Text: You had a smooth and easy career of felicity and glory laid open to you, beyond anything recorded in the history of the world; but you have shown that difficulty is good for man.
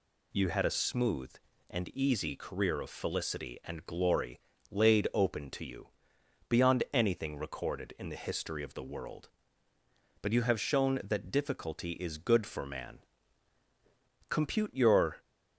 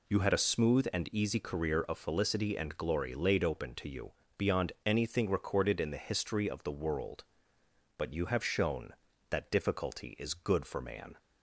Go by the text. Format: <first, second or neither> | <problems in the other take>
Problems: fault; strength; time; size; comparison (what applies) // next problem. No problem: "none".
second | pauses between "glory" and "laid"; slight; at 4.3 s; 0.32 s long // goes on to say "Compute your"; noticeable; from 14.2 s on; 0.88 s long